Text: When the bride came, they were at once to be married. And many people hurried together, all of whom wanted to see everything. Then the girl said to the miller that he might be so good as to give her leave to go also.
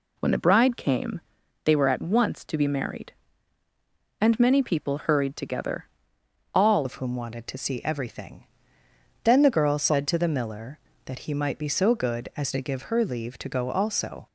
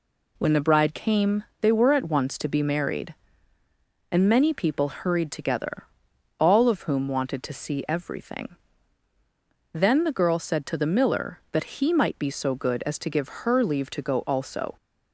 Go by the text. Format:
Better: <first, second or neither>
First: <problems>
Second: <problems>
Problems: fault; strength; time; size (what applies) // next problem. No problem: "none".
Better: second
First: changes voice at "of"; from 6.8 s on; 7.4 s long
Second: none